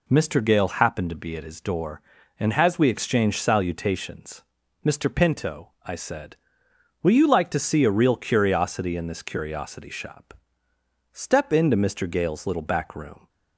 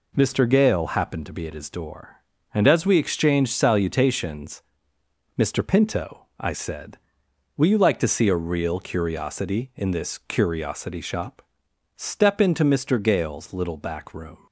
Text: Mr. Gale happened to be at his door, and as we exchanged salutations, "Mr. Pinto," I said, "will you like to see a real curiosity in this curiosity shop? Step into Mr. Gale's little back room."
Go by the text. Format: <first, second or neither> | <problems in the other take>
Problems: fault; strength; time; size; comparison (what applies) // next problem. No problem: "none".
neither | none